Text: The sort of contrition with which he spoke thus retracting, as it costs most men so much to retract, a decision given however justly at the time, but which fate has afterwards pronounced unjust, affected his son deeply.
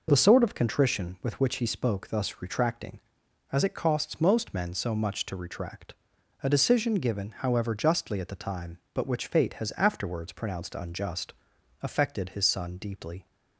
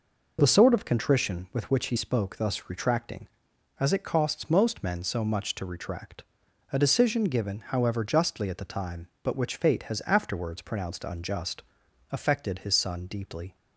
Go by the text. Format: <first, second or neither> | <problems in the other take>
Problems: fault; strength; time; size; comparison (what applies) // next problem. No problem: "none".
neither | none